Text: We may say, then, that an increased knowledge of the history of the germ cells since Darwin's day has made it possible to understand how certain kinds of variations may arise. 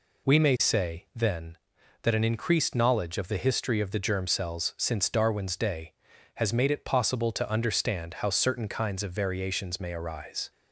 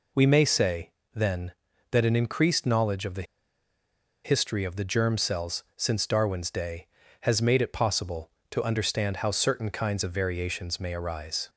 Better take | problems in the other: first | pauses between "the" and "history"; at 3.2 s; 1.0 s long

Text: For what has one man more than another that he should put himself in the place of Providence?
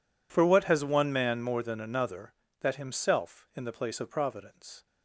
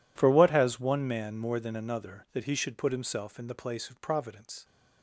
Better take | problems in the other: second | skips "he should put"; at 2.7 s

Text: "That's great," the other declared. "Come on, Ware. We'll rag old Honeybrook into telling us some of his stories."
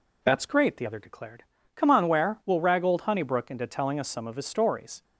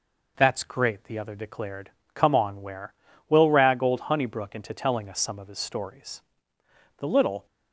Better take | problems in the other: first | goes on to say "The little"; slight; from 6.9 s on; 0.48 s long

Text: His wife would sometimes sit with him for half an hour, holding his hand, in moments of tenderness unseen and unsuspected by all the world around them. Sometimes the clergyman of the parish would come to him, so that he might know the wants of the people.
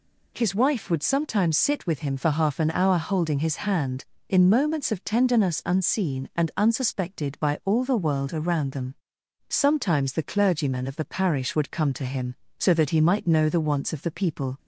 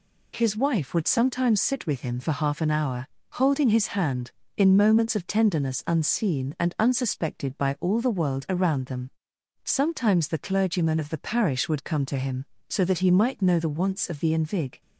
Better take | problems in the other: first | says "invig" for "people"; at 14.3 s

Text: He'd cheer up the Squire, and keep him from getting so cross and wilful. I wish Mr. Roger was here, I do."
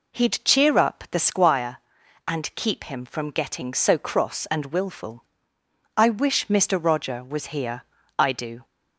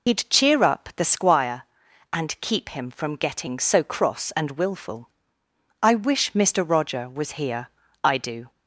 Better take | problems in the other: first | loses the start of "He'd"; at 0.0 s; 85 ms

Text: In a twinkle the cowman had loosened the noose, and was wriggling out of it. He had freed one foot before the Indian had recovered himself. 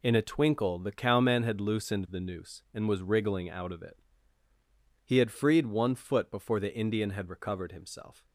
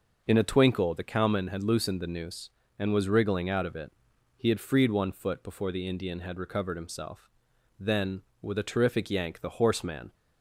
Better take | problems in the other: first | goes on to say "Then with a terrific yank the horseman"; strong; from 7.7 s on; 2.3 s long

